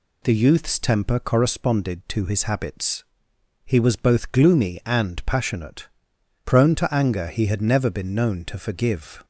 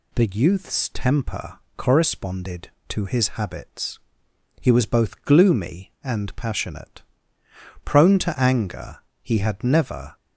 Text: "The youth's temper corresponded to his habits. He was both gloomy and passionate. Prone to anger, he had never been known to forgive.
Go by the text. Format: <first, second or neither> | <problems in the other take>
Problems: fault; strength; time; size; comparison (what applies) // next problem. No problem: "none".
first | pauses between "temper" and "corresponded"; slight; at 1.5 s; 0.20 s long // stops before "been known to forgive"; at 10.1 s